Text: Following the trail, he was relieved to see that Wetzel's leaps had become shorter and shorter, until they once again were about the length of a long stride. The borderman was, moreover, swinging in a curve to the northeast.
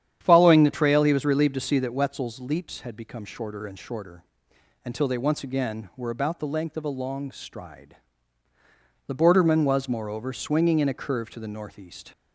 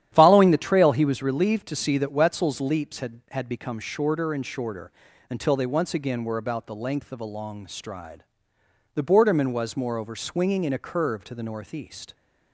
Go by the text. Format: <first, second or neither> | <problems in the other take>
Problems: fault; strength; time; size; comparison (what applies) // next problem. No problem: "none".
first | starts louder than the rest; strong; until 1.1 s; 11 dB; strong in the first // says "had" twice; at 3.3 s